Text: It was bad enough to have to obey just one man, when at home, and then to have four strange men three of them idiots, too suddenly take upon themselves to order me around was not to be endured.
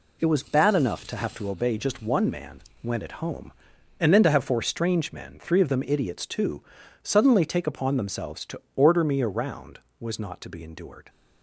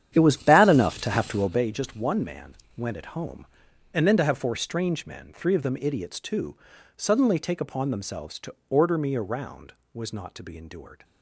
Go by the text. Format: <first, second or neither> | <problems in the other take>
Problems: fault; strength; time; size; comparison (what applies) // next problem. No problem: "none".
first | starts louder than the rest; strong; until 1.7 s; 9.5 dB // pauses between "too" and "suddenly"; at 6.5 s; 0.40 s long; also in the first // pauses between "to" and "order"; slight; at 8.5 s; 0.16 s long; slight in the first